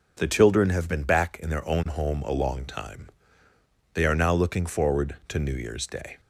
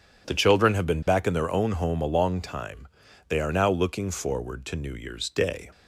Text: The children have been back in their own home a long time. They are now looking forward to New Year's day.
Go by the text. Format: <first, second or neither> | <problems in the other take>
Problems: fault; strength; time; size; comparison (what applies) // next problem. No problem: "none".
neither | none